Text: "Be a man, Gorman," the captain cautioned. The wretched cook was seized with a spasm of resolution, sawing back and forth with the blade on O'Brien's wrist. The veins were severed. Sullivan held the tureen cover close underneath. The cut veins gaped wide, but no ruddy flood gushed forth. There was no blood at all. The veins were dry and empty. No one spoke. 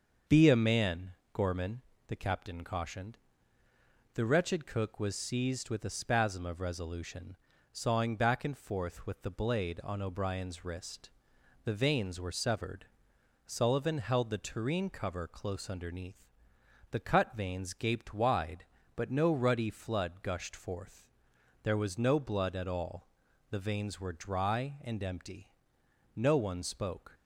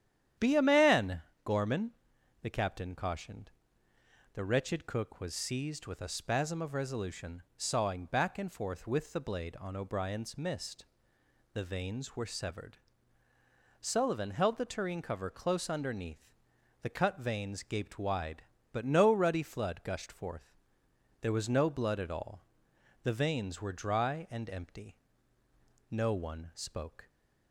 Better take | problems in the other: first | starts louder than the rest; strong; until 1.5 s; 10 dB; also in the first // says "mist" for "wrist"; at 10.3 s

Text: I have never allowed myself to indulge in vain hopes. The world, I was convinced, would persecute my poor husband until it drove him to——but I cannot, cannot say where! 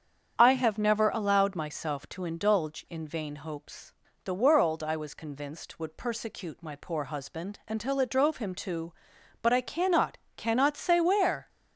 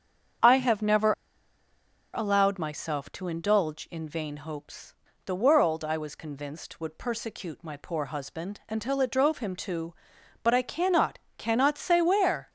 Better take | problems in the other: first | starts louder than the rest; strong; until 2.4 s; 8 dB; strong in the first // pauses between "never" and "allowed"; at 1.1 s; 1.0 s long

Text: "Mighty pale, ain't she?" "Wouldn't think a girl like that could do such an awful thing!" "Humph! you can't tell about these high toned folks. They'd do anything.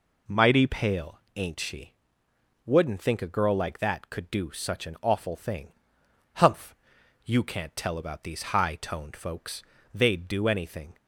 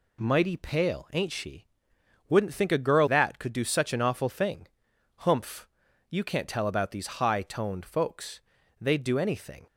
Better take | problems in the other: first | skips "like"; at 3.0 s

